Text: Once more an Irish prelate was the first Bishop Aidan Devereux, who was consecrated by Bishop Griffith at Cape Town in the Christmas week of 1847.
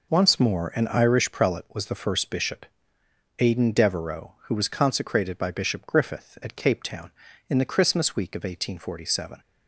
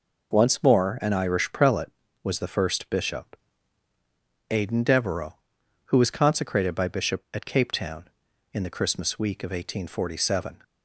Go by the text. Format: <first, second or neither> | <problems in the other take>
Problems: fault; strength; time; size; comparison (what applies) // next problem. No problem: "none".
first | pauses between "Bishop" and "Aidan"; at 3.3 s; 1.1 s long; noticeable in the first // skips "Griffith"; at 7.2 s